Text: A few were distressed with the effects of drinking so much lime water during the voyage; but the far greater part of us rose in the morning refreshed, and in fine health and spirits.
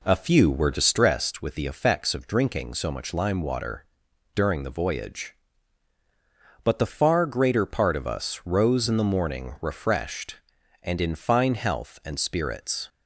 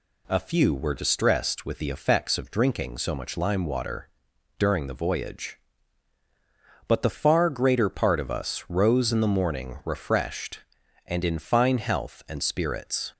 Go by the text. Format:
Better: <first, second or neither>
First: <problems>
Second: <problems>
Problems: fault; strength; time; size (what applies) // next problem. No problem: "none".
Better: second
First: starts louder than the rest; until 1.2 s; 3.5 dB // pauses between "water" and "during"; noticeable; at 3.8 s; 0.50 s long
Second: pauses between "water" and "during"; noticeable; at 4.0 s; 0.50 s long